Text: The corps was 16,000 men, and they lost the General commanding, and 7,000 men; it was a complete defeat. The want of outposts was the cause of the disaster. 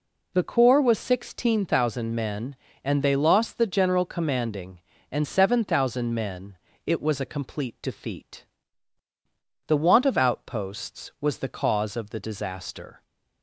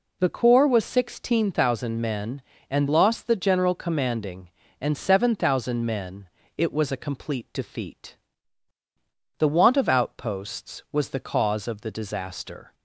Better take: first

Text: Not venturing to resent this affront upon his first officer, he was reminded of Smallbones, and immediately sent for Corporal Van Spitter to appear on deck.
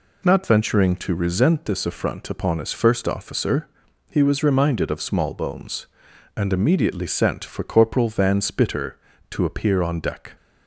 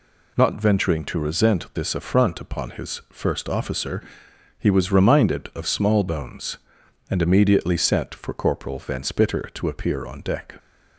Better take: neither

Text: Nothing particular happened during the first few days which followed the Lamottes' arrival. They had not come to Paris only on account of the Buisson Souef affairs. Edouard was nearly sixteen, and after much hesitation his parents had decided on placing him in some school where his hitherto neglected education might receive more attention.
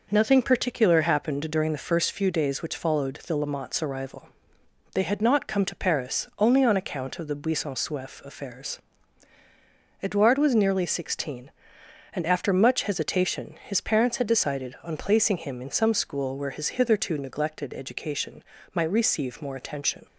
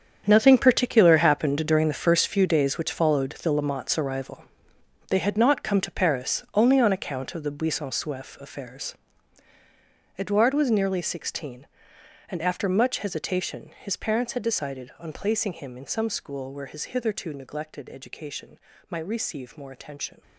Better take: first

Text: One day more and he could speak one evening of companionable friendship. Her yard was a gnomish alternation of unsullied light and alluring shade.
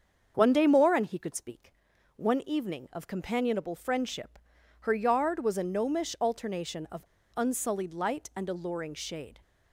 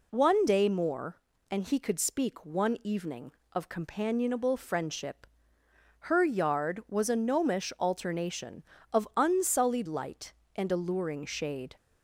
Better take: second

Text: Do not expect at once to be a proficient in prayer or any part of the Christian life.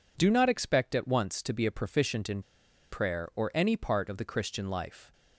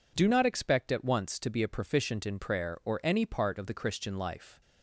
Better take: second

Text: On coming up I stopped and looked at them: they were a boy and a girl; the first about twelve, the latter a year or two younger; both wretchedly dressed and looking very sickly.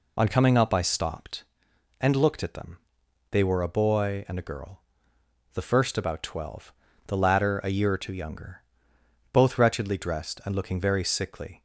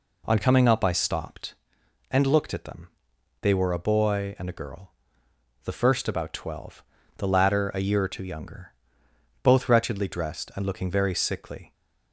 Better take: second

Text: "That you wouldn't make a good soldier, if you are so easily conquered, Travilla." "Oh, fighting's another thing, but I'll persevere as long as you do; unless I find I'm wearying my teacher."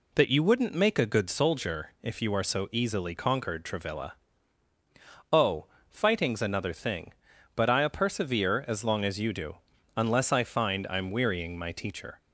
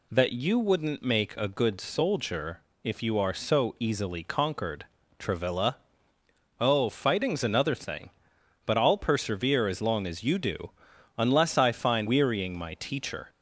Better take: first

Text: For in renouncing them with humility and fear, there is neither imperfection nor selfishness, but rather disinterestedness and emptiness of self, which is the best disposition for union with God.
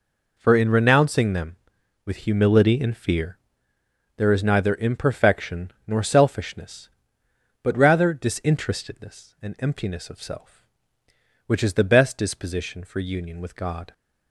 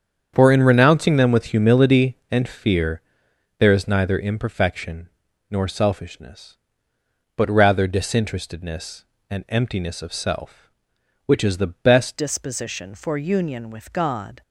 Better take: first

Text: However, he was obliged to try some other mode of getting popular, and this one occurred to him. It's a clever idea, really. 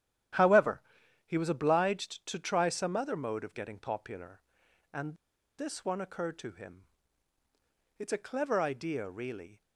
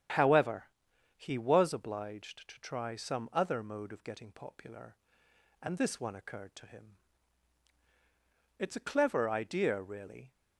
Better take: second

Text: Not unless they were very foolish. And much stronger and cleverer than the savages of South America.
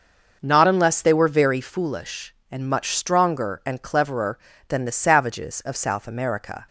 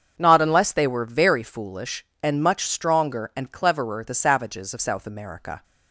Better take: first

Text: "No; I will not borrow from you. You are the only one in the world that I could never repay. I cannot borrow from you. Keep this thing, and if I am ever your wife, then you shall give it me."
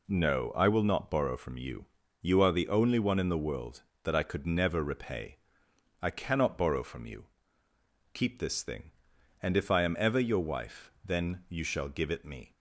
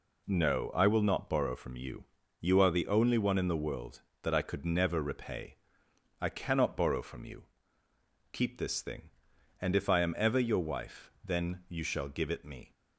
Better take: neither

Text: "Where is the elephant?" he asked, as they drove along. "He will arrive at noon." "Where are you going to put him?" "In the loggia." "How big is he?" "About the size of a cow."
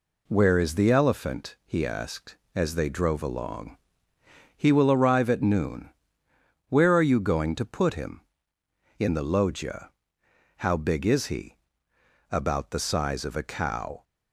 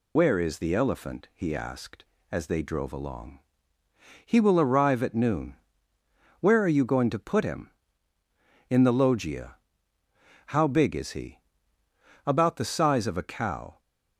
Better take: first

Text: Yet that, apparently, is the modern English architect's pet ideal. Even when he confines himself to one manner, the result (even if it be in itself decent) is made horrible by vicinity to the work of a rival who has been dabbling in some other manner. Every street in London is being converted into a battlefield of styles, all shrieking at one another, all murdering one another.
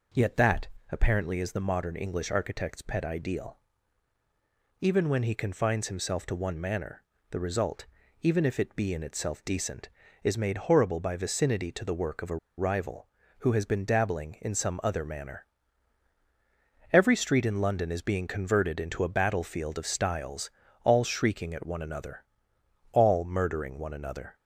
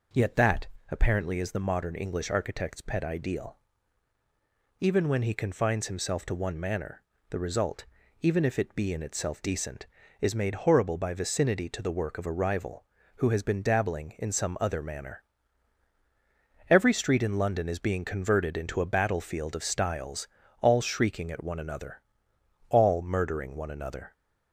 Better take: second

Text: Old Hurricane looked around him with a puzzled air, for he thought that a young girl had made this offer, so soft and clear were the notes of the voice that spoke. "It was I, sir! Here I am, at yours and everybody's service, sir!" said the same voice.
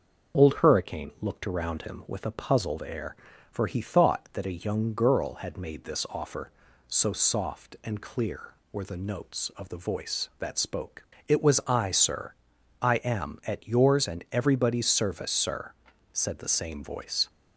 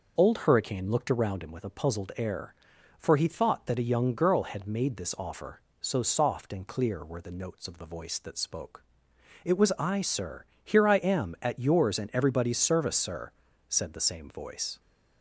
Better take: second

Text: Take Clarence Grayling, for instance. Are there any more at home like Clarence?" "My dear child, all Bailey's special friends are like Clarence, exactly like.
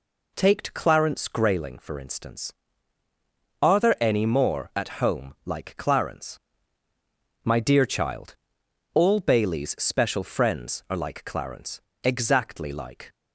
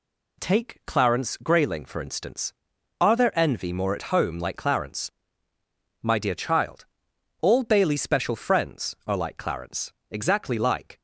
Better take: first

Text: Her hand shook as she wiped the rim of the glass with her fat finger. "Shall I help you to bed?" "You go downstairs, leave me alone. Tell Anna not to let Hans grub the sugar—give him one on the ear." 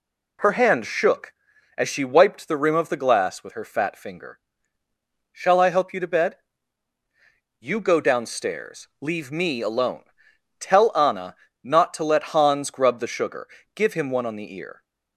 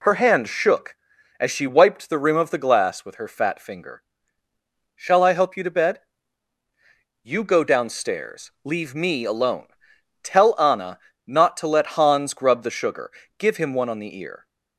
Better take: neither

